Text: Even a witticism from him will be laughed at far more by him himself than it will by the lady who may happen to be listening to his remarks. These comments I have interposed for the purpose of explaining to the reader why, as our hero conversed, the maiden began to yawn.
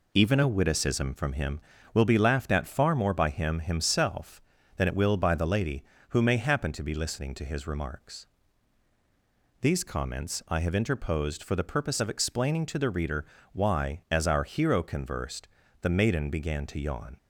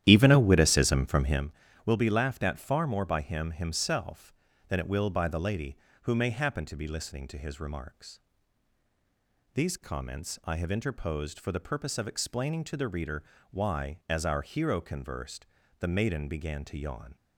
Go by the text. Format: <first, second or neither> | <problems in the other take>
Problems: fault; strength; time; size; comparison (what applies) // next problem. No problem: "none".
first | starts louder than the rest; strong; until 1.5 s; 11.5 dB // pauses between "reader" and "why"; slight; at 13.2 s; 0.28 s long; slight in the first